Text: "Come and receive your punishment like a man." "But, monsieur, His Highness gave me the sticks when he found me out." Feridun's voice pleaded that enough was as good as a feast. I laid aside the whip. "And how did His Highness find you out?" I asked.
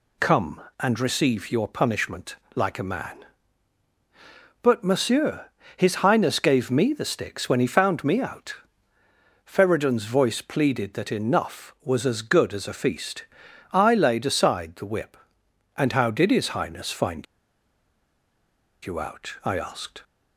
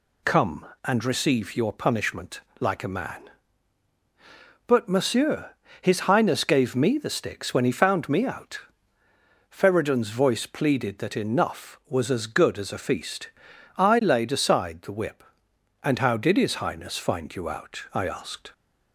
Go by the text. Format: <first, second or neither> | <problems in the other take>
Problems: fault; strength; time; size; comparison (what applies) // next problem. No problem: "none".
second | pauses between "punishment" and "like"; slight; at 2.3 s; 0.20 s long; slight in the second // pauses between "find" and "you"; strong; at 17.2 s; 1.6 s long